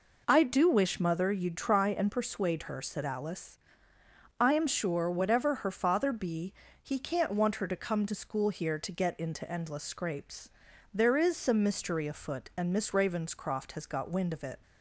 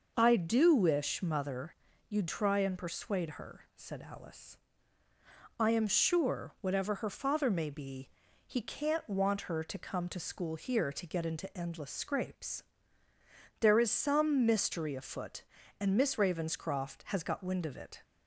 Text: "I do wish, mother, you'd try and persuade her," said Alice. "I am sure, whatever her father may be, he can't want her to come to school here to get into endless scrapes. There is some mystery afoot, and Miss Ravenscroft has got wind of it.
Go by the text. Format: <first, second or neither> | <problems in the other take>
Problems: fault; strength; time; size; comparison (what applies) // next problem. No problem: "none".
second | skips "may"; at 6.1 s